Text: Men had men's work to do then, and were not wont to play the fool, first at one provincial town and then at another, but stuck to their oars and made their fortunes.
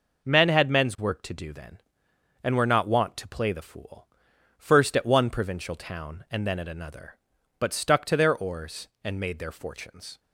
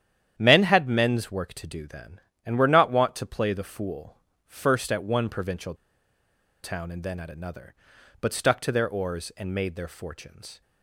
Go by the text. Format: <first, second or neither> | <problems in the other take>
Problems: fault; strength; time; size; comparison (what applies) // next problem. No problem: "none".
first | starts louder than the rest; strong; until 1.3 s; 10 dB // pauses between "provincial" and "town"; noticeable; at 5.7 s; 0.88 s long